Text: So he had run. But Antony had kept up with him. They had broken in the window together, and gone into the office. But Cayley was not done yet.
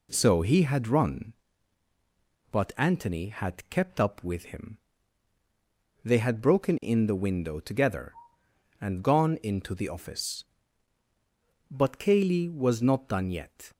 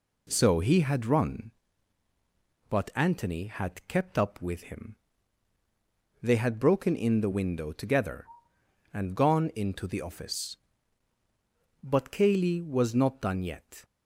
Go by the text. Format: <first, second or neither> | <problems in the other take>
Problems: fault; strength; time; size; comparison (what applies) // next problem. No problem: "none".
neither | none